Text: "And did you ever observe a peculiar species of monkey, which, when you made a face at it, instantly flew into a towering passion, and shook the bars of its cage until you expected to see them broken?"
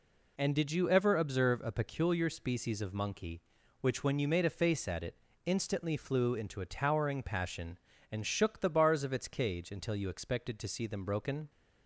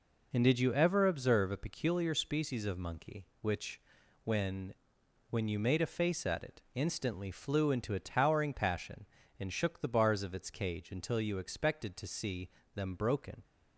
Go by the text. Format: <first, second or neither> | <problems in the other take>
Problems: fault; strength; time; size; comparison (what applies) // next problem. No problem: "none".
first | says "when" twice; at 5.2 s // pauses between "see" and "them"; slight; at 12.4 s; 0.24 s long